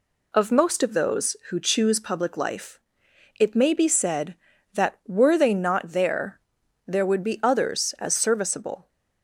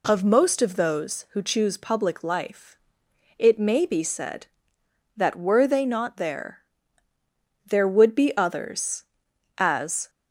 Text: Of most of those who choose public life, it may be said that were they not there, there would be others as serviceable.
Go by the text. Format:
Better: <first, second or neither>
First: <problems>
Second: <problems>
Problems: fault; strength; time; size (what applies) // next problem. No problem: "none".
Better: first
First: none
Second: stops before "serviceable"; at 10.0 s